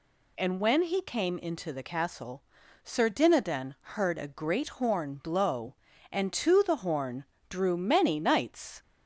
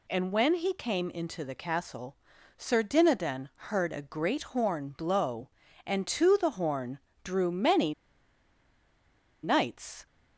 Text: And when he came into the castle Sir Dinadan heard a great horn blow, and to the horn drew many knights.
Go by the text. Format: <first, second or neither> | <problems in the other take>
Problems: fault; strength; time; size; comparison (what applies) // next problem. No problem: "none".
first | pauses between "castle" and "Sir"; at 2.1 s; 0.40 s long; also in the first // pauses between "horn" and "drew"; slight; at 6.9 s; 0.26 s long; slight in the first // pauses between "many" and "knights"; strong; at 7.9 s; 1.4 s long